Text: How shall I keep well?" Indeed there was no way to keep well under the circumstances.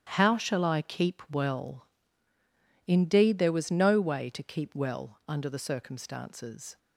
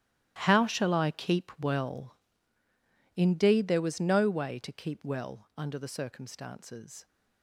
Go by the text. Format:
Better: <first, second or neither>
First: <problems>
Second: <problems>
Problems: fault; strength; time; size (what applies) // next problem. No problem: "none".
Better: first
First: starts louder than the rest; strong; until 1.1 s; 11 dB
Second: gets quieter; strong; throughout; 16 dB // starts louder than the rest; strong; until 1.4 s; 14.5 dB